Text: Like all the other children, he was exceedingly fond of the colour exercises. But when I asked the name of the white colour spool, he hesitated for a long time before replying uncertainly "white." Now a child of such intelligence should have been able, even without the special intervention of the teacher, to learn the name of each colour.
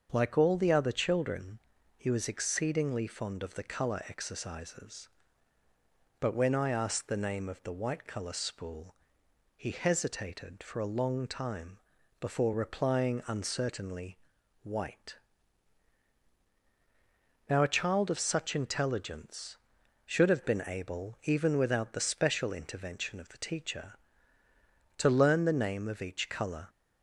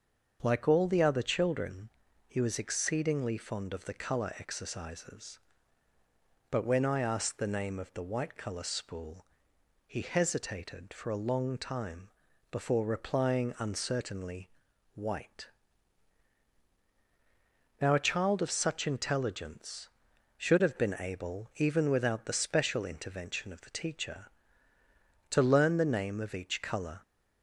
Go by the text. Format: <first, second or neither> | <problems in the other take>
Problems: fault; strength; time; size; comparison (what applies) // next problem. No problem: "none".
neither | starts louder than the rest; the same in both // pauses between "time" and "before"; the same in both // pauses between "uncertainly" and "white"; noticeable; the same in both